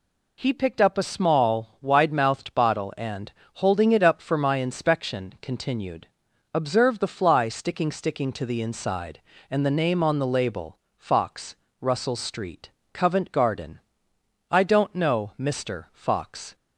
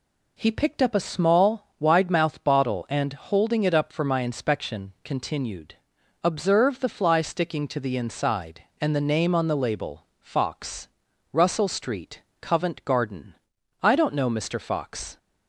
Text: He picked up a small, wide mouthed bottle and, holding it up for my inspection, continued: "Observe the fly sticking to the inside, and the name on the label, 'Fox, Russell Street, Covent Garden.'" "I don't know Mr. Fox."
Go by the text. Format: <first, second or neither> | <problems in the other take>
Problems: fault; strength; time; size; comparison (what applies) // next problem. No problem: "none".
second | says "sticking" twice; at 7.9 s